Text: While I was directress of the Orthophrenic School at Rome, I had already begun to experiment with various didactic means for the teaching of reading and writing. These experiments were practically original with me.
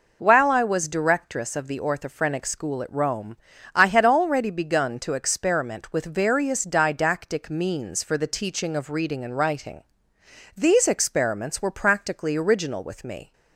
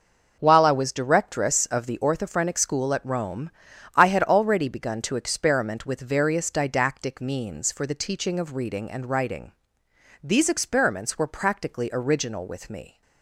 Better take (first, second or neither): neither